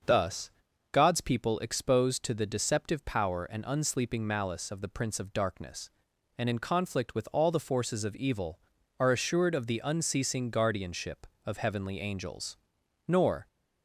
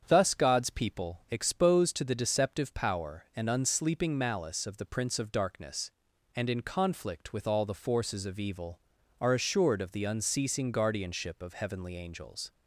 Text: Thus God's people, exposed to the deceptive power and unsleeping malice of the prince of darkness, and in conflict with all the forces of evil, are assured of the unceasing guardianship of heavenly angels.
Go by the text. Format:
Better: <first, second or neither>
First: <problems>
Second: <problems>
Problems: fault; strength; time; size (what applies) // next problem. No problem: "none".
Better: second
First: starts louder than the rest; until 1.4 s; 6.5 dB // pauses between "Thus" and "God's"; at 0.5 s; 0.40 s long // goes on to say "Nor"; slight; from 13.0 s on; 0.40 s long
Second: starts louder than the rest; strong; until 1.0 s; 8 dB